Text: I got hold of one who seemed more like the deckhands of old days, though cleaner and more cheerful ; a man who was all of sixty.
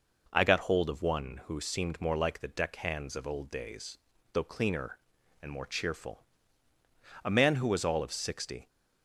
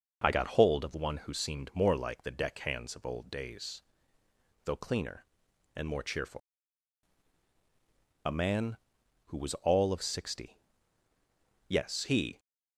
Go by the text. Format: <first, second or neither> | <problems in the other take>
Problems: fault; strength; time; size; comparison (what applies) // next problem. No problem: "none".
first | goes on to say "Yes he"; noticeable; from 11.6 s on; 0.70 s long